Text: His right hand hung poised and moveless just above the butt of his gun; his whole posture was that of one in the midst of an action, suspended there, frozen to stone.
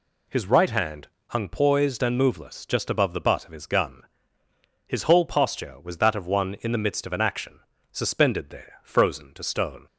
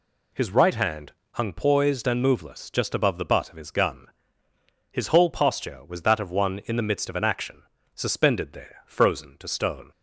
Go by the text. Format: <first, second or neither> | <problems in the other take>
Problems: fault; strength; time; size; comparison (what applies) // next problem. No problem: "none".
neither | pauses between "hand" and "hung"; slight; the same in both